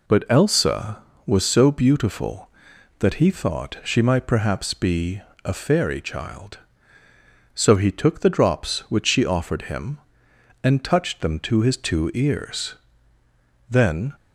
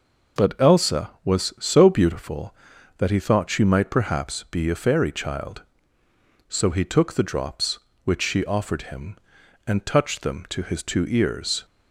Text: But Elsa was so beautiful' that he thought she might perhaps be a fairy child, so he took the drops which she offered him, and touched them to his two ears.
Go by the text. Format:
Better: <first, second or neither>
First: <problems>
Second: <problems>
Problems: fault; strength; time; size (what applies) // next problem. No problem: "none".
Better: second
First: pauses between "be" and "a"; slight; at 5.2 s; 0.24 s long // goes on to say "Then"; slight; from 13.6 s on; 0.44 s long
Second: none